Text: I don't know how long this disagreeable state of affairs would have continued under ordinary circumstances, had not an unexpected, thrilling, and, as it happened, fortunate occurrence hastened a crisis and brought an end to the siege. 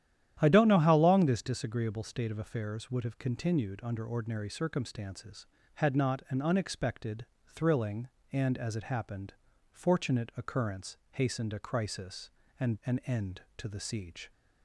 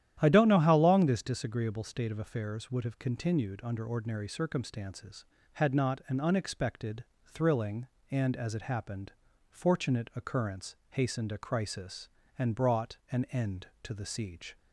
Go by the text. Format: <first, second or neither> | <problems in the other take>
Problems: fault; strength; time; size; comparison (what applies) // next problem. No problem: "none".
second | starts louder than the rest; strong; until 1.4 s; 11 dB; strong in the second // pauses between "occurrence" and "hastened"; slight; at 10.9 s; 0.16 s long; slight in the second // skips "brought"; at 12.8 s